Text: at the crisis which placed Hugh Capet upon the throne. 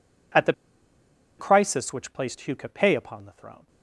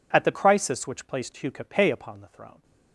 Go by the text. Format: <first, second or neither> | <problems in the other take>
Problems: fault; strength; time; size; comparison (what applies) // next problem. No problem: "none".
second | pauses between "the" and "crisis"; noticeable; at 0.5 s; 0.85 s long